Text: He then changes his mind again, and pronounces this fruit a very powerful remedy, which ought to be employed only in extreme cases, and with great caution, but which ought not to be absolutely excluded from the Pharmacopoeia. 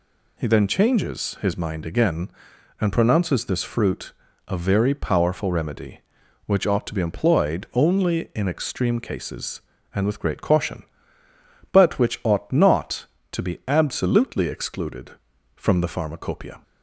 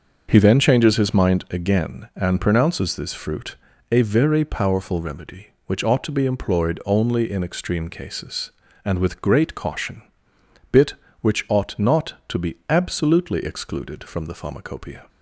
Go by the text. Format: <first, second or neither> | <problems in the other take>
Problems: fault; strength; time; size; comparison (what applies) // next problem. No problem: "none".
first | starts louder than the rest; until 1.3 s; 6.5 dB // pauses between "fruit" and "a"; slight; at 3.5 s; 0.34 s long; slight in the first // says "bit" for "but"; at 10.6 s